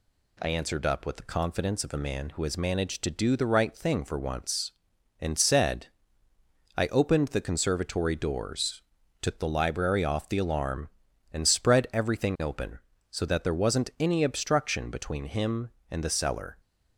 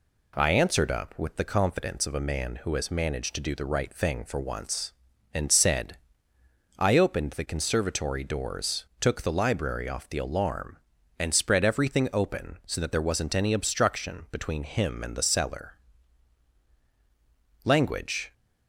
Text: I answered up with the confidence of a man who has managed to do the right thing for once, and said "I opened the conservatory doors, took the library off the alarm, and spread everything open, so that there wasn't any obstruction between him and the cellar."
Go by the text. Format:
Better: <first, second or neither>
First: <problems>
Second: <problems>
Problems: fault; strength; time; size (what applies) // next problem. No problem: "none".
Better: first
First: pauses between "said" and "I"; noticeable; at 5.8 s; 0.88 s long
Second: pauses between "said" and "I"; noticeable; at 5.9 s; 0.80 s long // goes on to say "Language"; noticeable; from 17.6 s on; 0.70 s long